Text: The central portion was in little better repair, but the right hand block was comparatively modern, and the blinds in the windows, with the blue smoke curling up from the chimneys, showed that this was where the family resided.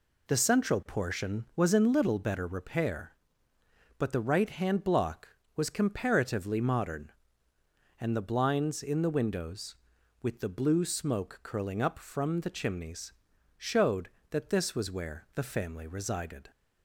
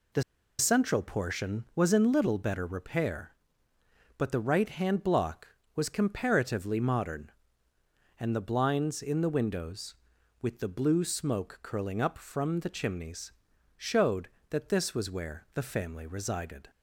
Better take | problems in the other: first | pauses between "The" and "central"; at 0.2 s; 0.36 s long

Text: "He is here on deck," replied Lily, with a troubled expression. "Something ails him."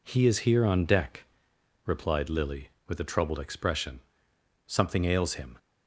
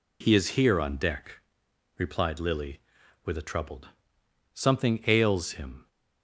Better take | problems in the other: first | skips "expression"; at 4.2 s

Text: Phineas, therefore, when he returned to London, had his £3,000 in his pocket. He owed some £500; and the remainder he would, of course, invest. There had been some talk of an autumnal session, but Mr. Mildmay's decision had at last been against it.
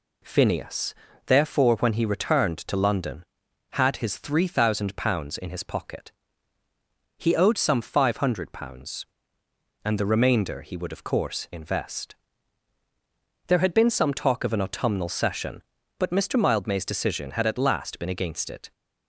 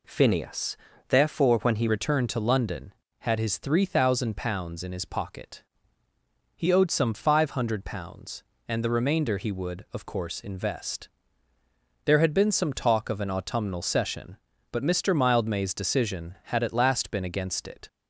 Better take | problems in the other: first | changes voice at "returned"; from 1.8 s on; 16.0 s long

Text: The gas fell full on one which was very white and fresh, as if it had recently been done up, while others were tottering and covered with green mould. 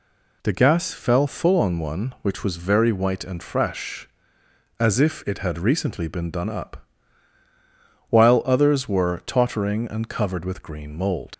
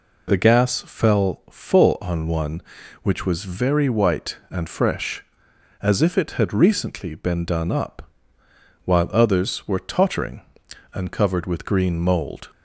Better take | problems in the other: second | leaves "mould" unfinished; at 11.3 s; 105 ms

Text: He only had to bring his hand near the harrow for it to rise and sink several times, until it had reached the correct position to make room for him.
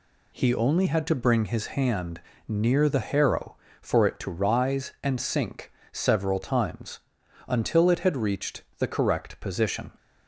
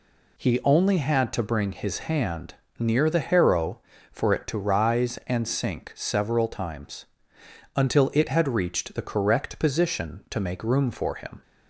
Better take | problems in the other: second | pauses between "hand" and "near"; slight; at 2.1 s; 0.28 s long; slight in the second // pauses between "sink" and "several"; slight; at 5.7 s; 0.20 s long // pauses between "reached" and "the"; slight; at 8.6 s; 0.16 s long // stops before "to make room for him"; at 9.9 s

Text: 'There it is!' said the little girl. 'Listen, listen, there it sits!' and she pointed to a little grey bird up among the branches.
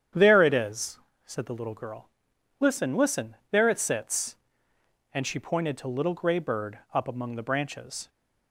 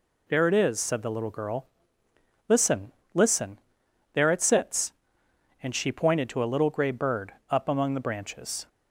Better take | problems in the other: second | starts louder than the rest; strong; until 1.4 s; 9 dB // skips "a"; at 5.8 s // pauses between "bird" and "up"; slight; at 6.7 s; 0.16 s long; slight in the second

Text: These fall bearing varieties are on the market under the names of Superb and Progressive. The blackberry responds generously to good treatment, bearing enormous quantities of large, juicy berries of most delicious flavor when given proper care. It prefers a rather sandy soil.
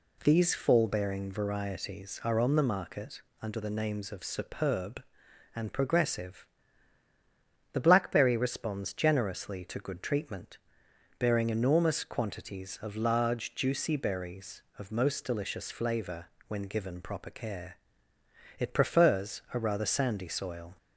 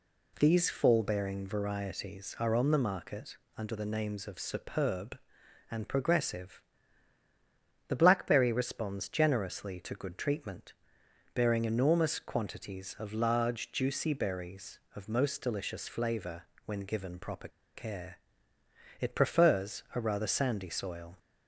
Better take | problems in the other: first | pauses between "market" and "under"; slight; at 3.3 s; 0.20 s long; slight in the first // pauses between "flavor" and "when"; slight; at 16.4 s; 0.22 s long; slight in the first // pauses between "proper" and "care"; slight; at 17.4 s; 0.26 s long

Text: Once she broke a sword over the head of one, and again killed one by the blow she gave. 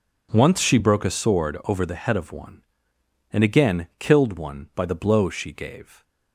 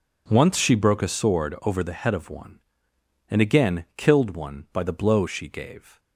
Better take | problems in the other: neither | none

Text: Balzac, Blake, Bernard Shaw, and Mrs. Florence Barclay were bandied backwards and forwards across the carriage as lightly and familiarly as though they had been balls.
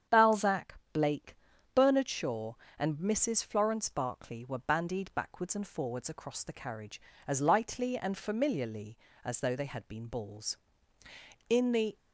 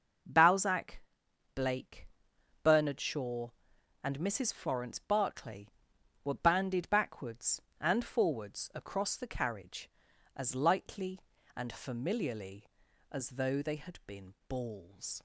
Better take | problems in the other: second | starts louder than the rest; strong; until 1.2 s; 8.5 dB; also in the second // goes on to say "In the"; slight; from 11.4 s on; 0.48 s long

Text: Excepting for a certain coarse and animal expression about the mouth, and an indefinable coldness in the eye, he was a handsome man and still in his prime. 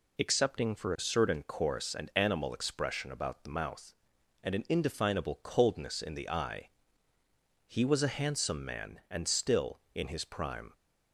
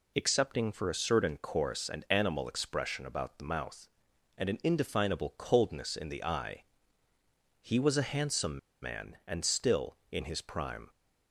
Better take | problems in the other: first | pauses between "handsome" and "man"; slight; at 8.5 s; 0.22 s long

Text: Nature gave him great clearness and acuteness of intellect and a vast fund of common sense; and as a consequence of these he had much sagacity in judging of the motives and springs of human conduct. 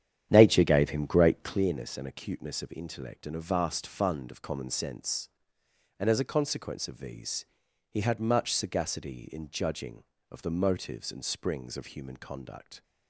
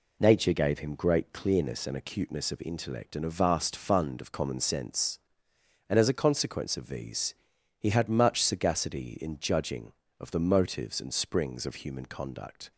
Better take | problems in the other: second | starts louder than the rest; strong; until 1.7 s; 10 dB // pauses between "these" and "he"; at 7.4 s; 0.42 s long; also in the second

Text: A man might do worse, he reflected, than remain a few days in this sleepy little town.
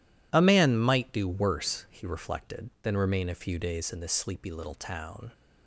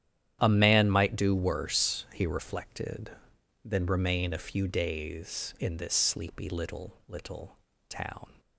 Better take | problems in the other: first | starts louder than the rest; strong; until 1.4 s; 10.5 dB // says "little" twice; at 7.0 s

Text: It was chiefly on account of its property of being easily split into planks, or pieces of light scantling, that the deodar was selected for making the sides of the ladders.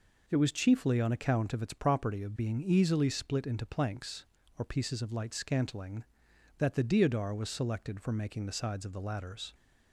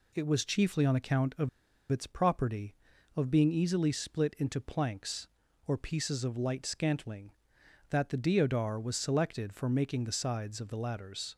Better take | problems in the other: first | pauses between "of" and "its"; at 1.4 s; 0.42 s long

